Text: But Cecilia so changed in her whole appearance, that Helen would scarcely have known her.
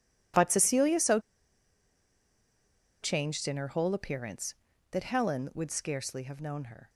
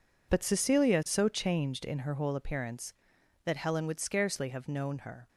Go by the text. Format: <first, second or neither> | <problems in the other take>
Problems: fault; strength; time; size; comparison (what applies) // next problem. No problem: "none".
second | pauses between "so" and "changed"; strong; at 1.2 s; 1.8 s long